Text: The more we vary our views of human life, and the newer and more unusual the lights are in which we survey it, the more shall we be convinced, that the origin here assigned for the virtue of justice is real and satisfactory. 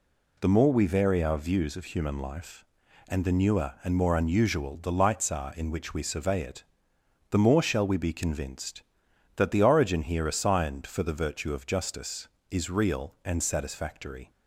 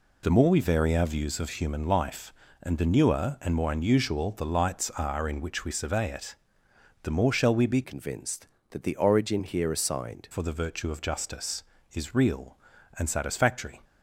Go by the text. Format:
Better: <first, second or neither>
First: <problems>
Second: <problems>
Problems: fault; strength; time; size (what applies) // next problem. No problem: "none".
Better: first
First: none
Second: changes voice from "convinced" to "assigned"; from 7.8 to 10.2 s; 2.4 s long